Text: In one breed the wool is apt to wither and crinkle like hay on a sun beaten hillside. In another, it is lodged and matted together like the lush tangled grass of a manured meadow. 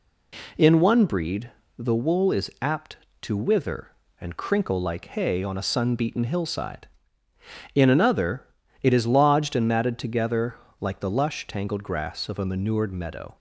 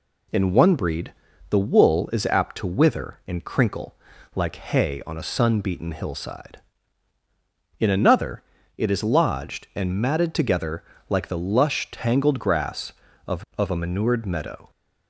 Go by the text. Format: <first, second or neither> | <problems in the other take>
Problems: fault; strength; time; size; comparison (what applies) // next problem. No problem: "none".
first | pauses between "breed" and "the"; at 1.1 s; 0.38 s long; slight in the first // pauses between "crinkle" and "like"; at 3.9 s; 0.38 s long // pauses between "together" and "like"; slight; at 10.8 s; 0.26 s long; slight in the first // says "of" twice; at 13.5 s